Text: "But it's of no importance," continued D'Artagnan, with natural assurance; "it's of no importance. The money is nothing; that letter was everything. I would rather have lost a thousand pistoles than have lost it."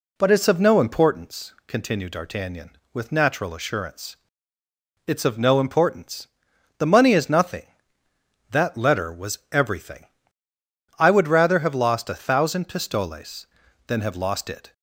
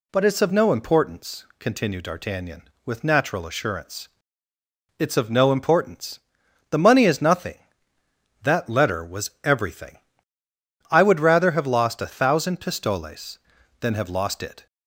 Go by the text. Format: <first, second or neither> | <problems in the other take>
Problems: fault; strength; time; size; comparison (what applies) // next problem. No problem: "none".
second | starts louder than the rest; slight; until 1.1 s; 2 dB